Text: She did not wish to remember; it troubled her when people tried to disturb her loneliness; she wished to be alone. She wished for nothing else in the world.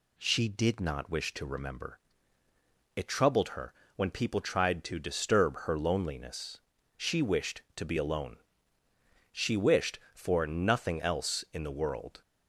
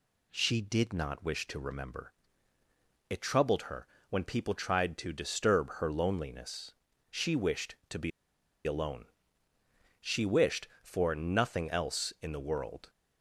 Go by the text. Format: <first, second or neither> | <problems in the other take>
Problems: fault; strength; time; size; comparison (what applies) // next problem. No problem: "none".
first | pauses between "her" and "when"; slight; at 3.8 s; 0.22 s long; slight in the first // pauses between "be" and "alone"; noticeable; at 8.1 s; 0.55 s long